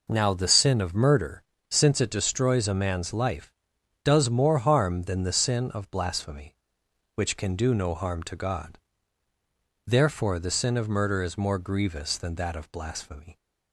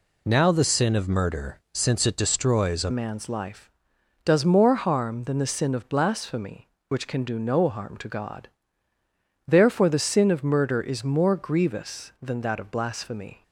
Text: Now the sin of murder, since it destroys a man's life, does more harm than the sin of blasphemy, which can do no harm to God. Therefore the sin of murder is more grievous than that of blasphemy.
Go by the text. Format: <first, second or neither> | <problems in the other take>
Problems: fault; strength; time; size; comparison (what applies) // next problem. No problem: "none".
first | changes voice at "man's"; from 2.9 s on; 10.5 s long